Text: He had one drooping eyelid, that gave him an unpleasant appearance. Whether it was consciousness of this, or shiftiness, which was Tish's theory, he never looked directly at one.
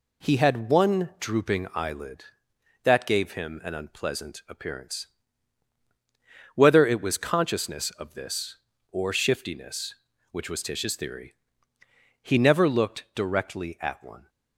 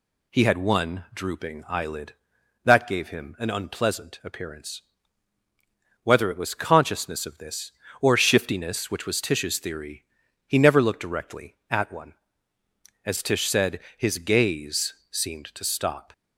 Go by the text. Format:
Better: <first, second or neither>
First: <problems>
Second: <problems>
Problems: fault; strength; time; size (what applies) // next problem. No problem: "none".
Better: first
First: none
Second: goes on to say "As Tish said his gaze seemed to stop"; strong; from 13.0 s on; 3.0 s long